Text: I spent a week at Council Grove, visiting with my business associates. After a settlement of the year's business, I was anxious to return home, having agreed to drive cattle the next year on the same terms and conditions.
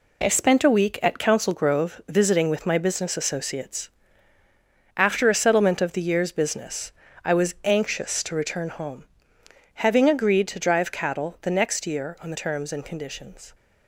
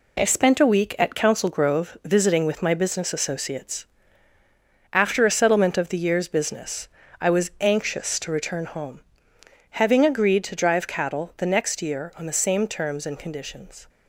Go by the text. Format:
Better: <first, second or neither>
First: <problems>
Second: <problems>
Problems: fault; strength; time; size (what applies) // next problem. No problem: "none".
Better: second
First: skips "same"; at 12.3 s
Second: none